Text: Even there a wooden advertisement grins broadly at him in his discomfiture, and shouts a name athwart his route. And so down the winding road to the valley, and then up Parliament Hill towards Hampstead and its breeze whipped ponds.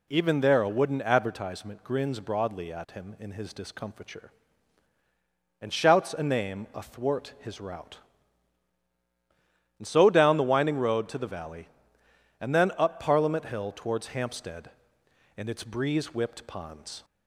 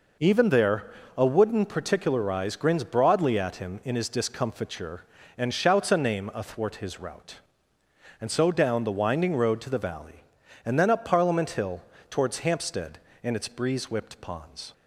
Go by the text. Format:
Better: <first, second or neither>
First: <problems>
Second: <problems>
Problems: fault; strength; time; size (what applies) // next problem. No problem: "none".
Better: first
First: none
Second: pauses between "there" and "a"; slight; at 0.8 s; 0.26 s long // says "particularize" for "advertisement"; at 1.6 s // pauses between "Hill" and "towards"; slight; at 11.8 s; 0.28 s long